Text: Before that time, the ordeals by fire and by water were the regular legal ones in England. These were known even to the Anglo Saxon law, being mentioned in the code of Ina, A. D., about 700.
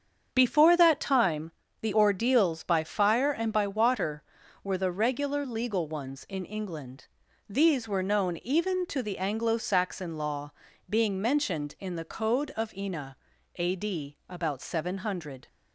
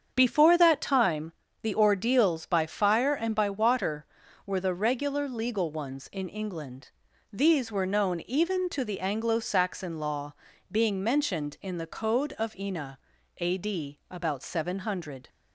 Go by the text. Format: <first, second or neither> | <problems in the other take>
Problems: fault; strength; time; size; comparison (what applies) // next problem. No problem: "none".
neither | starts louder than the rest; strong; the same in both